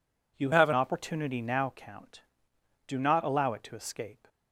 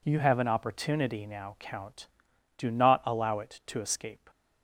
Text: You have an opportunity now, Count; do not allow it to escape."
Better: second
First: changes voice from "have" to "an"; from 0.5 to 0.7 s; 0.2 s long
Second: none

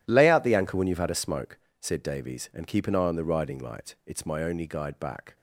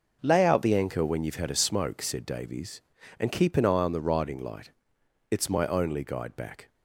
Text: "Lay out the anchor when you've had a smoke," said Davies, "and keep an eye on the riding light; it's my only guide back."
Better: second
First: gets quieter; strong; throughout; 14 dB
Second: none

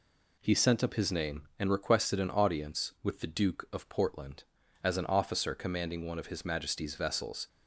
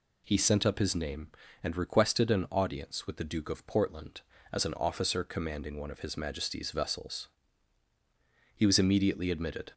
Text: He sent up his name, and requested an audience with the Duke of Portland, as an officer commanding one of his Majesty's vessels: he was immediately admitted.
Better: second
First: stops before "he was immediately admitted"; at 7.4 s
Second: none

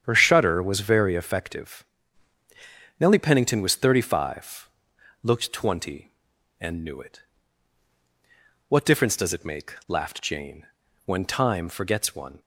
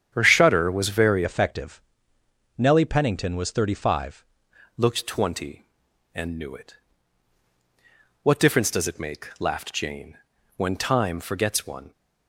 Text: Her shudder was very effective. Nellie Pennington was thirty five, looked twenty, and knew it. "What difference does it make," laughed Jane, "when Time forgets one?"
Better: first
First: starts louder than the rest; strong; until 1.0 s; 9 dB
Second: starts louder than the rest; strong; until 1.1 s; 8.5 dB // changes voice from "effective" to "five"; from 1.2 to 4.2 s; 3.0 s long

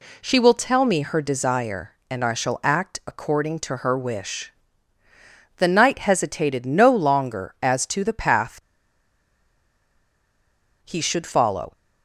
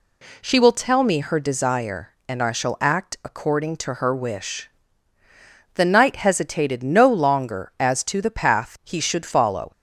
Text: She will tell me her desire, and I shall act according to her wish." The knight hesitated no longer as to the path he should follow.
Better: second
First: pauses between "path" and "he"; strong; at 8.6 s; 2.2 s long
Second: none

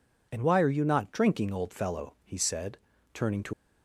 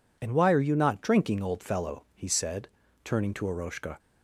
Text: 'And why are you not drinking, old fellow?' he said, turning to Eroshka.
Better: second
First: stops before "Eroshka"; at 3.5 s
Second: none

